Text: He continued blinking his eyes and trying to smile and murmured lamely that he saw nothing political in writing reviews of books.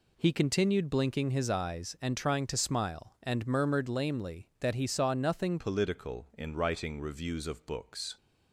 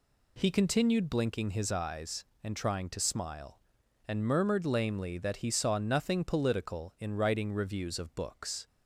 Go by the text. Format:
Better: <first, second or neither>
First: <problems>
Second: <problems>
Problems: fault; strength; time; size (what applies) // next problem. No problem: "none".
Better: second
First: changes voice at "political"; from 5.5 s on; 2.6 s long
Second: none